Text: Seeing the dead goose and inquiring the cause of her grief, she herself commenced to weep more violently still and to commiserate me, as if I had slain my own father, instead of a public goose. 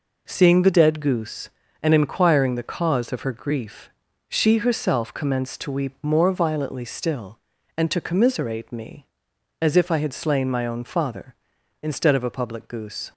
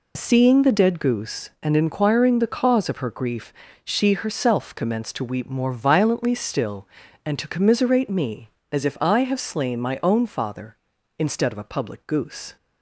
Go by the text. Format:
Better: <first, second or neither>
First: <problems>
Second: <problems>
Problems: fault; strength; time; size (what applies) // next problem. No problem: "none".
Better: first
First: none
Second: says "have" for "had"; at 9.2 s